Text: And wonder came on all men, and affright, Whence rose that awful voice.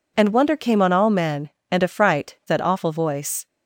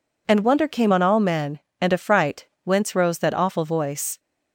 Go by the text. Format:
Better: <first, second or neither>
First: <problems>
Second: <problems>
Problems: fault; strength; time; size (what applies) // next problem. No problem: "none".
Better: second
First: skips "Whence rose"; at 2.4 s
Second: none